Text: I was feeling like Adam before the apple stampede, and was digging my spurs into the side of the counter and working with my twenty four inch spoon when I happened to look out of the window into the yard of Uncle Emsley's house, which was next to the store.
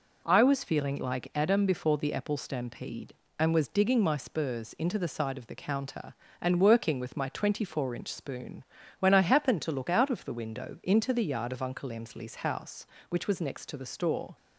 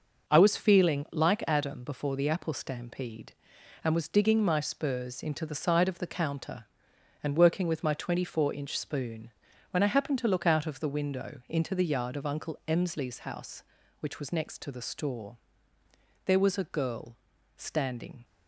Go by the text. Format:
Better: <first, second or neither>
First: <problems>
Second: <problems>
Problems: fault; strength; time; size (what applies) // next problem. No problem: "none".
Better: first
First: pauses between "spoon" and "when"; slight; at 8.6 s; 0.36 s long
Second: pauses between "spoon" and "when"; at 9.3 s; 0.40 s long // goes on to say "There was a girl standing"; strong; from 16.2 s on; 2.0 s long